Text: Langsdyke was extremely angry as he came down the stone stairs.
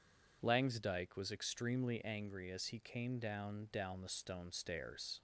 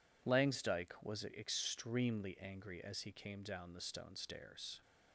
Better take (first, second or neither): second